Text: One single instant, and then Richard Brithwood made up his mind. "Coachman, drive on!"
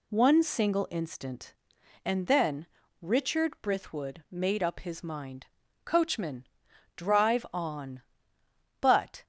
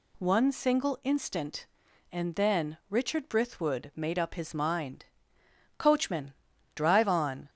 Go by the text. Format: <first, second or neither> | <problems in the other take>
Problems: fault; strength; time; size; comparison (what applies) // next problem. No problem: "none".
second | pauses between "then" and "Richard"; slight; at 2.6 s; 0.34 s long // goes on to say "But"; slight; from 8.8 s on; 0.42 s long